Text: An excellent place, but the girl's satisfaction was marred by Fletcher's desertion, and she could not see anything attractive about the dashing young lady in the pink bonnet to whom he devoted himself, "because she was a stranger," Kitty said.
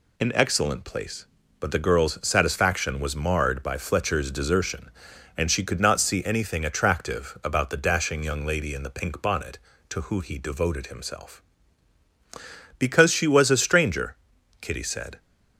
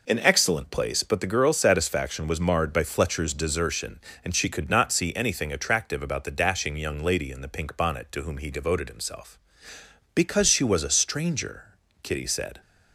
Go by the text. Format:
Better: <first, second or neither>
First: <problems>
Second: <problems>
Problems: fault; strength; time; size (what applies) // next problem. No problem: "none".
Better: second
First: says "who" for "whom"; at 10.0 s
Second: none